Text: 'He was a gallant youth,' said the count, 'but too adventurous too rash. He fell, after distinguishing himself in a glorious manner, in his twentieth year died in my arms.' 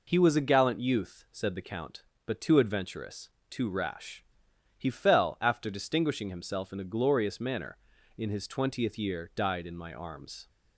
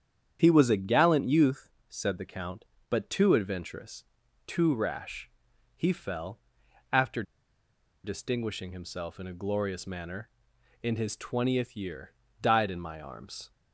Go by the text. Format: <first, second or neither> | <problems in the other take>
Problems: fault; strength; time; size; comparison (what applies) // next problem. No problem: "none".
first | starts louder than the rest; strong; until 1.4 s; 8.5 dB // pauses between "adventurous" and "too"; at 4.0 s; 0.42 s long; slight in the first // pauses between "after" and "distinguishing"; noticeable; at 7.2 s; 0.81 s long // pauses between "year" and "died"; slight; at 12.1 s; 0.28 s long